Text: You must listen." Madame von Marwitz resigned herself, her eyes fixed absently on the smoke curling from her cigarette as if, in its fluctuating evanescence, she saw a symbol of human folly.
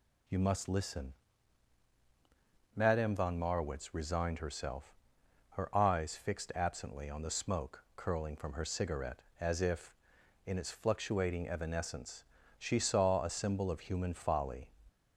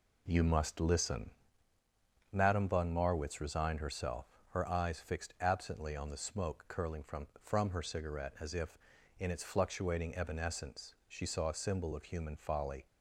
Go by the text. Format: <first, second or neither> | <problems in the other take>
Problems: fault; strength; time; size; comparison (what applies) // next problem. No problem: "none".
first | says "from" twice; at 7.4 s